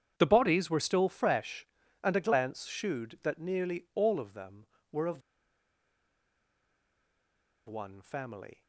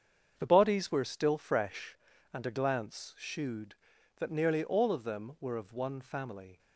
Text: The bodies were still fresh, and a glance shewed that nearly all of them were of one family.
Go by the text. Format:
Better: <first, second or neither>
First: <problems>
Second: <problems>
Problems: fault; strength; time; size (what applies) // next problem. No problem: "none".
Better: second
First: starts louder than the rest; strong; until 1.1 s; 8.5 dB // pauses between "of" and "one"; strong; at 5.2 s; 2.4 s long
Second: starts louder than the rest; strong; until 1.3 s; 7.5 dB